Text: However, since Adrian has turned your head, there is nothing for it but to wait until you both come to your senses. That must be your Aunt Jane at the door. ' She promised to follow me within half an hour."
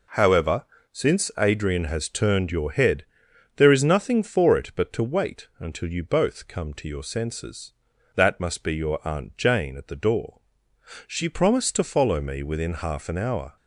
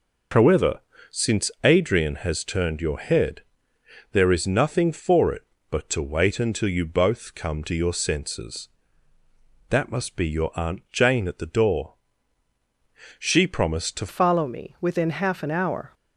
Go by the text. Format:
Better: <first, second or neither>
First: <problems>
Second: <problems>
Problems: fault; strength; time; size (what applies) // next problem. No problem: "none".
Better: first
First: none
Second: changes voice at "follow"; from 14.0 s on; 1.9 s long